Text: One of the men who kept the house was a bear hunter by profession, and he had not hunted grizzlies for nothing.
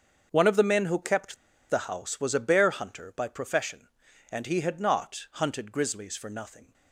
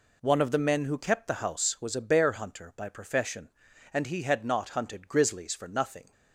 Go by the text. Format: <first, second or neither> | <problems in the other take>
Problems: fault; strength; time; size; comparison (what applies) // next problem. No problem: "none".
second | starts louder than the rest; until 1.3 s; 7 dB // pauses between "kept" and "the"; slight; at 1.3 s; 0.34 s long